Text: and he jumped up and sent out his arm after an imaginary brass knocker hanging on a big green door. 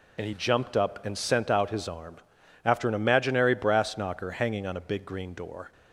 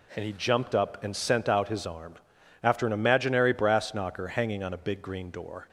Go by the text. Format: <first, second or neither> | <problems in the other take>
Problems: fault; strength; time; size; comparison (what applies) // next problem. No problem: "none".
second | loses the start of "and"; at 0.1 s; 60 ms // pauses between "arm" and "after"; noticeable; at 2.1 s; 0.50 s long; noticeable in the second